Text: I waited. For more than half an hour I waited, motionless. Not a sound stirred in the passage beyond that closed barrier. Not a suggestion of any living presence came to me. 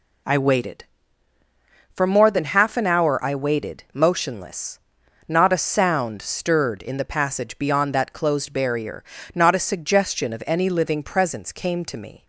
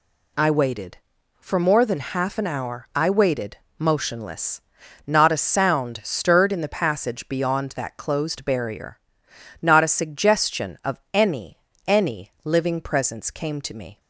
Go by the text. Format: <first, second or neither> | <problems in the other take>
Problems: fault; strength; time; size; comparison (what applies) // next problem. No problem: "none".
first | says "any" twice; at 11.8 s